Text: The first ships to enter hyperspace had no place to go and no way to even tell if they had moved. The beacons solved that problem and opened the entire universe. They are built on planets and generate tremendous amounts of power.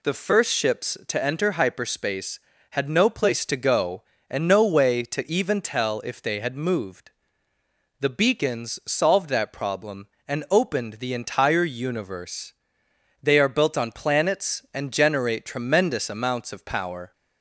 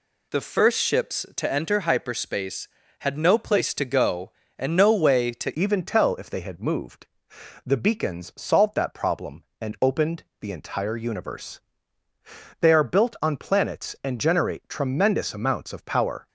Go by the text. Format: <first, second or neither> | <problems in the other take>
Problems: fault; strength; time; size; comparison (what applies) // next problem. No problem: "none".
first | changes voice at "even"; from 5.5 s on; 10.7 s long // pauses between "opened" and "the"; slight; at 10.2 s; 0.16 s long